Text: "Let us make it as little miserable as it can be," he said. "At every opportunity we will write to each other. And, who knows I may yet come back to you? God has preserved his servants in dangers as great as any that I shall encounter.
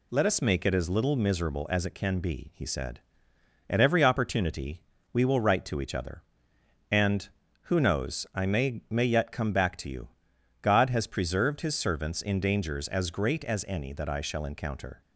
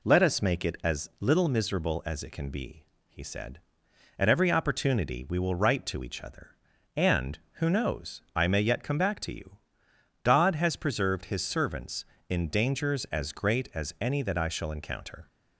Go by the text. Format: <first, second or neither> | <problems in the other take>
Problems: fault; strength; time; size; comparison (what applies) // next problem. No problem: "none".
second | pauses between "opportunity" and "we"; slight; at 4.8 s; 0.30 s long // says "may" twice; at 8.8 s